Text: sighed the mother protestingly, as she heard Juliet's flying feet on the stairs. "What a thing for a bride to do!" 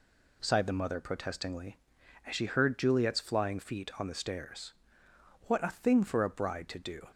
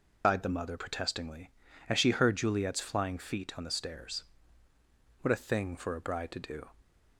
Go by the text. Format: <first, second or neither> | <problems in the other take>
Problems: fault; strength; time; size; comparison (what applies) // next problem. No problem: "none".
first | loses the start of "sighed"; at 0.2 s; 150 ms